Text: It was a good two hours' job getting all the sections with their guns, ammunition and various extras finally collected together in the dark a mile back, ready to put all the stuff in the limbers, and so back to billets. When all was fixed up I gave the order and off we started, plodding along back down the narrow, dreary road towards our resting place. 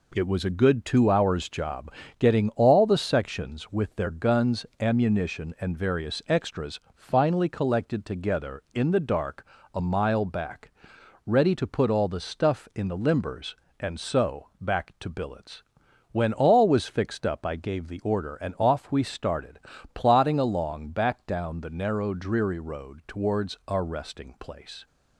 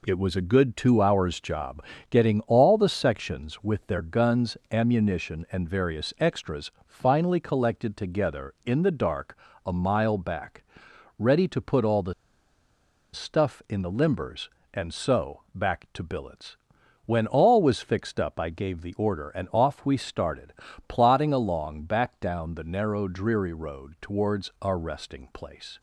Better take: first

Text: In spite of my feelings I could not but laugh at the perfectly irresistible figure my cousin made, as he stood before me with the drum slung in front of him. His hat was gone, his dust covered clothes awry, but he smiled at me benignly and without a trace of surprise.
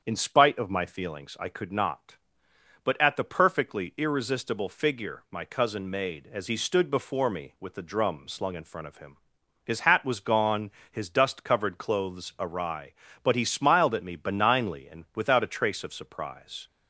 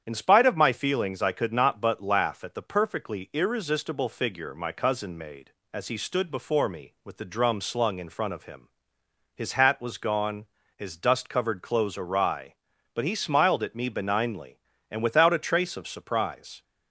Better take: second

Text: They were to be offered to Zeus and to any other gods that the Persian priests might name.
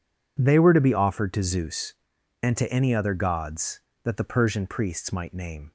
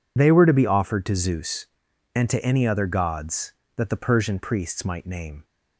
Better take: first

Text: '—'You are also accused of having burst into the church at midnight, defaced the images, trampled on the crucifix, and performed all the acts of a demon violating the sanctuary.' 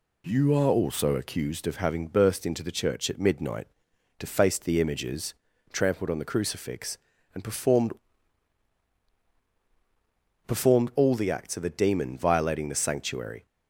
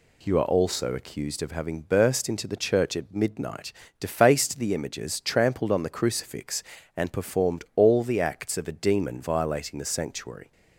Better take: second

